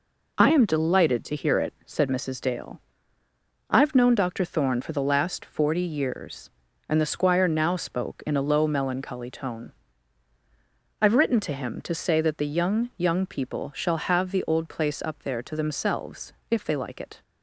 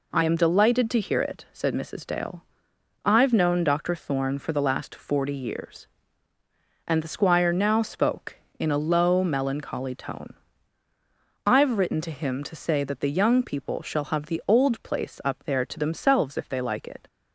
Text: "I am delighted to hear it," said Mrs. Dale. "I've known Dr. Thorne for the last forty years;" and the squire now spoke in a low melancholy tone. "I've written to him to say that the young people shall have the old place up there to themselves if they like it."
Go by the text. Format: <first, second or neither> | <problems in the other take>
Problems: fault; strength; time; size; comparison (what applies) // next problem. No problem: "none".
second | says "young" twice; at 12.9 s // pauses between "themselves" and "if"; slight; at 16.3 s; 0.16 s long